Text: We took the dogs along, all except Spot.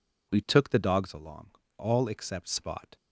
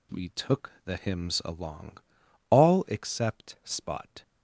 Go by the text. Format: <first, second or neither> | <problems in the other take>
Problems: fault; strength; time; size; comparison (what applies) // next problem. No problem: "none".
first | says "hymns" for "dogs"; at 0.9 s